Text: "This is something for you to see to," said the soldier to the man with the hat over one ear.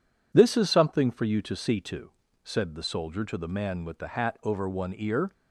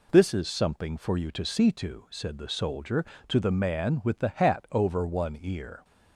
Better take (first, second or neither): neither